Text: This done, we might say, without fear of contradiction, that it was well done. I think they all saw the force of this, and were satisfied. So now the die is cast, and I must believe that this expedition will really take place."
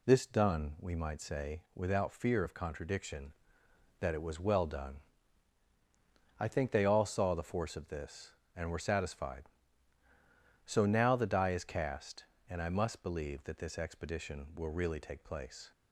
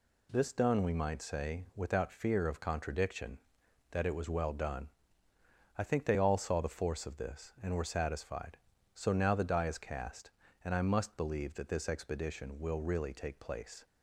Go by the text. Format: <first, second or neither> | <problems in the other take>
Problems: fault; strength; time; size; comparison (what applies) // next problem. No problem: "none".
neither | none